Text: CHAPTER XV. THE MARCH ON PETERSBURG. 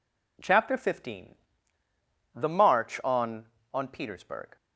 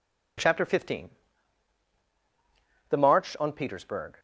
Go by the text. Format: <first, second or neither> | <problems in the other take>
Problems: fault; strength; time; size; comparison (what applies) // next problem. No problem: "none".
second | says "ON" twice; at 3.7 s